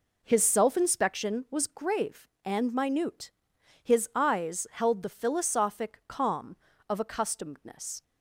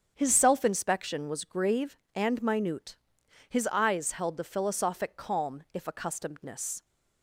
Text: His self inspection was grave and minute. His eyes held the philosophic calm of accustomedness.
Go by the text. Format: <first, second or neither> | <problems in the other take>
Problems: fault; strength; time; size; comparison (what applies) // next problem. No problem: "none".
first | starts louder than the rest; strong; until 1.1 s; 7.5 dB // says "if" for "of"; at 5.7 s